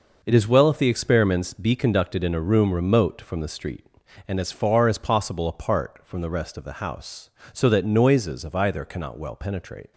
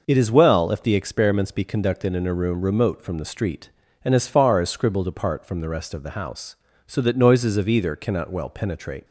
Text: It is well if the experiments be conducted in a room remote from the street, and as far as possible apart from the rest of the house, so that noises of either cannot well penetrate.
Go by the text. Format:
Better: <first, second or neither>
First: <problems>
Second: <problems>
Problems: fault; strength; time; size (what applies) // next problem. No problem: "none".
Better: first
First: none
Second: says "scribbled" for "possible"; at 4.6 s